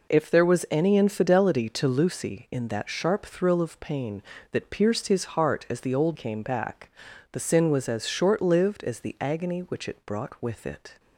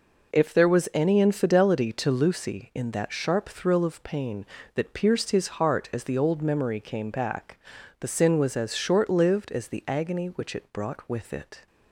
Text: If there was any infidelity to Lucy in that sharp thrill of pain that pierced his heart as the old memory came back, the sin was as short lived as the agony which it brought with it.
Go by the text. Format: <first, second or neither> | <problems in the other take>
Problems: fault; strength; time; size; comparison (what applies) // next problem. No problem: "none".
second | skips "memory"; at 6.1 s